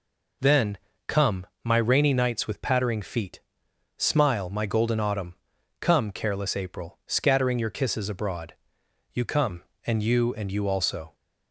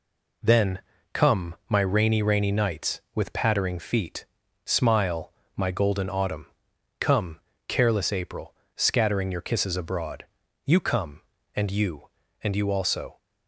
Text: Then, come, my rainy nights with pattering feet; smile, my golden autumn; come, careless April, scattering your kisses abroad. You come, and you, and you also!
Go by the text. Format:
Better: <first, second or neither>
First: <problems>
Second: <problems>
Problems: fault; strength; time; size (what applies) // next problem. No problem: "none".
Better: first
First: none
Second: says "rainy" twice; at 2.2 s